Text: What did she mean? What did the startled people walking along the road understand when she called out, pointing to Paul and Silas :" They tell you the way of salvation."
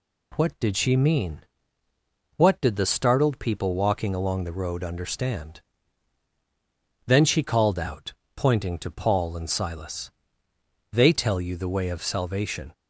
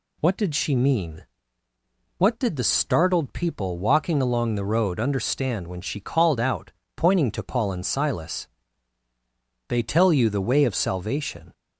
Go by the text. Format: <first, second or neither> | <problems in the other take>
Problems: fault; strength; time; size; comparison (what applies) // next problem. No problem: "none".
second | says "then" for "when"; at 7.0 s